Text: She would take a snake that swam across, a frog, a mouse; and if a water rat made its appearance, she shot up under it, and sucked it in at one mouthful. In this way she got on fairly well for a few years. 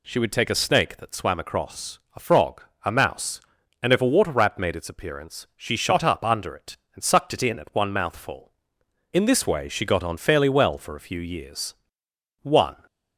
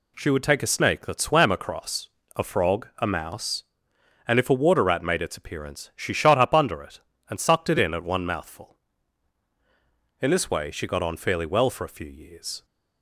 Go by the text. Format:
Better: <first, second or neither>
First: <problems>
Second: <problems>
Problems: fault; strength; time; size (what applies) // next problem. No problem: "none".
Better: second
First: goes on to say "One"; slight; from 12.4 s on; 0.32 s long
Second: none